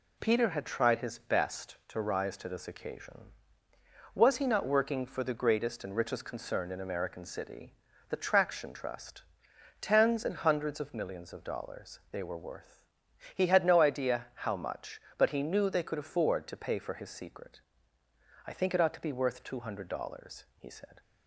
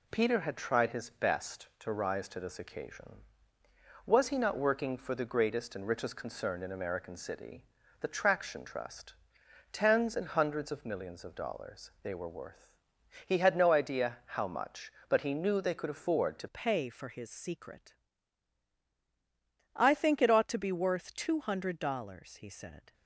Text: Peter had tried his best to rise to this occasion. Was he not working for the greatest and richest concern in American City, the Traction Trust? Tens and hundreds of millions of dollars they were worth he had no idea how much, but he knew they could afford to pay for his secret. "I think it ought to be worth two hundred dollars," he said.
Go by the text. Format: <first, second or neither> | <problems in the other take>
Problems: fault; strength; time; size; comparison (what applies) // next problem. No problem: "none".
first | pauses between "worth" and "he"; noticeable; at 12.7 s; 0.54 s long; noticeable in the first // changes voice at "pay"; from 16.4 s on; 6.5 s long